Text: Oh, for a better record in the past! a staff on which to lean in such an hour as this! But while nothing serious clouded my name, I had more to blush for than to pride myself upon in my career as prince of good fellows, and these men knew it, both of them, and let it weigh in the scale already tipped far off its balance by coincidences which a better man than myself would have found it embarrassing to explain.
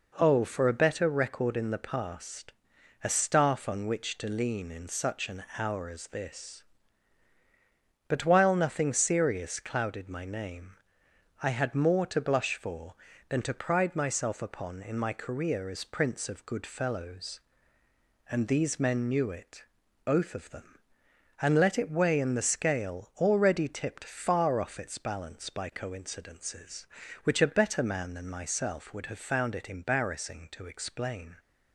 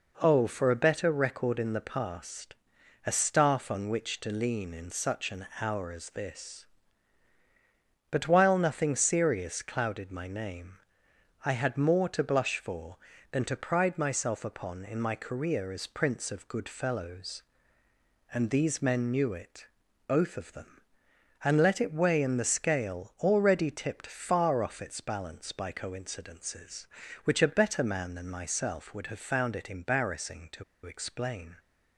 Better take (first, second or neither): first